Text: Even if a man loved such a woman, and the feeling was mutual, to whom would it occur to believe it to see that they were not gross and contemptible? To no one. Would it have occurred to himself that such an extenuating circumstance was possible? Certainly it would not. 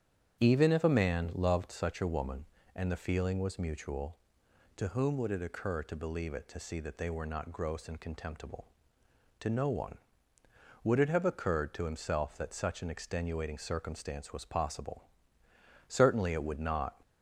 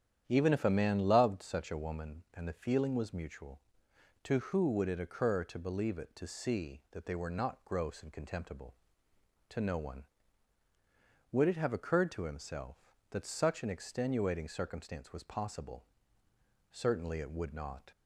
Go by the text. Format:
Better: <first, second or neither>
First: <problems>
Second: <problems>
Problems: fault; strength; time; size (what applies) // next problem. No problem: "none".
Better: first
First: starts louder than the rest; strong; until 1.4 s; 9 dB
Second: starts louder than the rest; strong; until 1.2 s; 10 dB // says "who" for "whom"; at 4.3 s